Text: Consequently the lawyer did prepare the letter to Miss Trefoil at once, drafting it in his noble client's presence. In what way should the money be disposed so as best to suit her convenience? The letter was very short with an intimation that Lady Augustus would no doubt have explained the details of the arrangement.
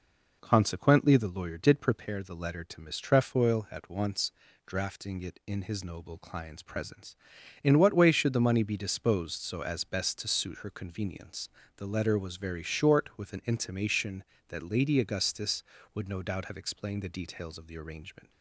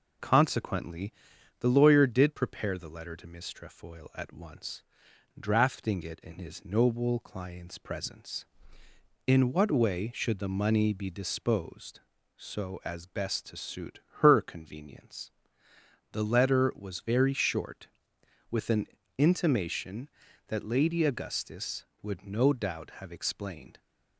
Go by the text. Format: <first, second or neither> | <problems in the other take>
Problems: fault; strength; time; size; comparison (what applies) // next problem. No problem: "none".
first | pauses between "Consequently" and "the"; noticeable; at 1.1 s; 0.48 s long // pauses between "suit" and "her"; slight; at 14.0 s; 0.18 s long // pauses between "an" and "intimation"; slight; at 18.8 s; 0.30 s long // stops before "the details of the arrangement"; at 23.7 s